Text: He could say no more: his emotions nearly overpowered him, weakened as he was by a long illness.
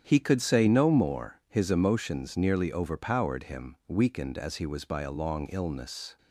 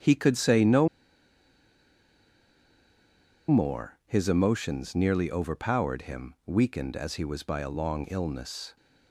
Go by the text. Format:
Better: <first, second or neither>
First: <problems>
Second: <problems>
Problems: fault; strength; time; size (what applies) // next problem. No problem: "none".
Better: first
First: starts louder than the rest; strong; until 1.0 s; 8.5 dB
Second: starts louder than the rest; strong; until 3.6 s; 8.5 dB // pauses between "no" and "more"; strong; at 0.8 s; 2.6 s long